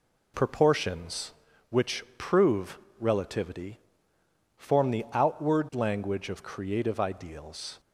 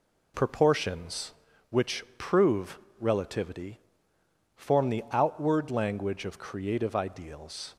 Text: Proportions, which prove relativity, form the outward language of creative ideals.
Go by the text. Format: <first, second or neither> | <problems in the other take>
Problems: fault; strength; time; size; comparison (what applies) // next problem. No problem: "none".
neither | pauses between "prove" and "relativity"; slight; the same in both